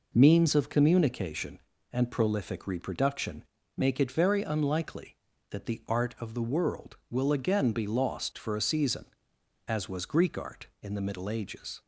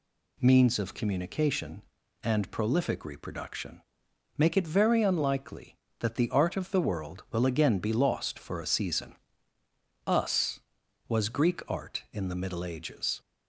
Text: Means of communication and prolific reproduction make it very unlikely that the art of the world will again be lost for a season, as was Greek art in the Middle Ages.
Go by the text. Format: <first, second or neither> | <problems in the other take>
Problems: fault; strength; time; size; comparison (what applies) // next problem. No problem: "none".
first | pauses between "reproduction" and "make"; noticeable; at 3.8 s; 0.56 s long; slight in the first // says "us" for "as"; at 10.0 s